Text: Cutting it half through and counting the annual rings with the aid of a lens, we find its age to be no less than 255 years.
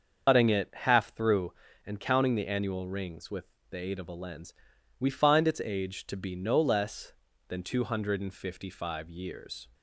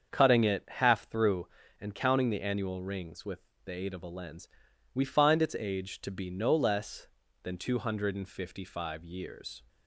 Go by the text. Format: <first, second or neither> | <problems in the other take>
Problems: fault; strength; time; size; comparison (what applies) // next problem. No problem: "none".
second | loses the start of "Cutting"; at 0.2 s; 110 ms // starts louder than the rest; until 1.3 s; 6.5 dB; strong in the second // pauses between "with" and "the"; slight; at 3.4 s; 0.26 s long; slight in the second